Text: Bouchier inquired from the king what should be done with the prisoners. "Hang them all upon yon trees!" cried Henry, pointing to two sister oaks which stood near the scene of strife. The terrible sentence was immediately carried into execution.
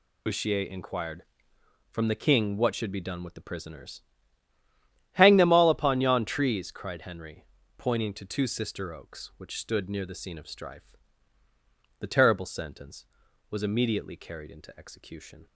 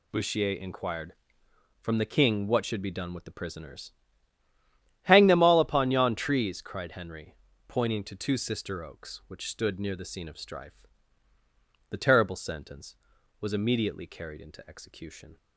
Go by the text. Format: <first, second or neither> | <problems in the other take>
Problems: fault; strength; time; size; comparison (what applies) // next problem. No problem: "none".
second | loses the start of "Bouchier"; at 0.2 s; 35 ms